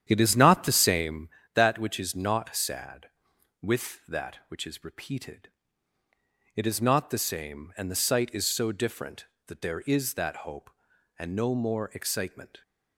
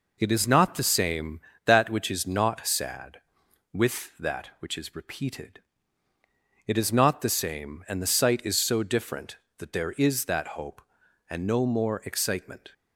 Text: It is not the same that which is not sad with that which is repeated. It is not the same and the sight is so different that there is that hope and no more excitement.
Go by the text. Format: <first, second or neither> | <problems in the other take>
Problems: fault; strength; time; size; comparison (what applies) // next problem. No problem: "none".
second | starts louder than the rest; strong; until 1.2 s; 9.5 dB